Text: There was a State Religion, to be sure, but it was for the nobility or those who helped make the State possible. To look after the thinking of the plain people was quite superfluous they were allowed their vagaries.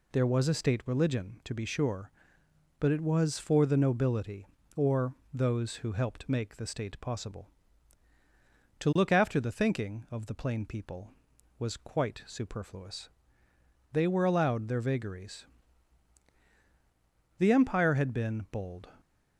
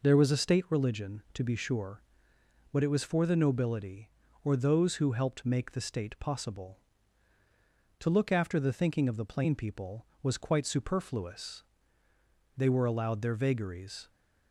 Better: second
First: pauses between "or" and "those"; slight; at 5.1 s; 0.20 s long // pauses between "superfluous" and "they"; noticeable; at 13.0 s; 0.84 s long // goes on to say "The Empire had been bold"; from 17.3 s on; 1.4 s long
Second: pauses between "superfluous" and "they"; noticeable; at 11.6 s; 0.94 s long

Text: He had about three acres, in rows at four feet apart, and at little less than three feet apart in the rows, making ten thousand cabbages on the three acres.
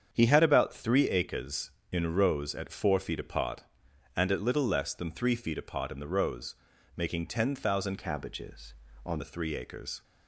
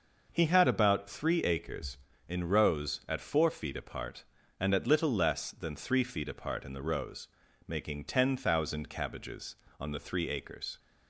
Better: second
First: starts louder than the rest; strong; until 1.1 s; 7.5 dB // changes voice from "cabbages" to "on"; from 7.9 to 9.2 s; 1.3 s long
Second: none

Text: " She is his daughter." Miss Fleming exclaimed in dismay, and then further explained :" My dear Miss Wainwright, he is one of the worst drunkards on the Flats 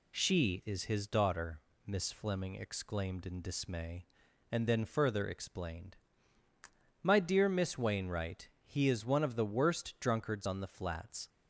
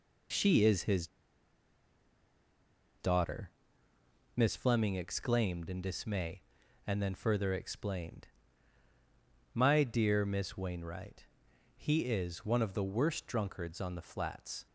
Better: first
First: none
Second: pauses between "his" and "daughter"; strong; at 1.0 s; 1.9 s long

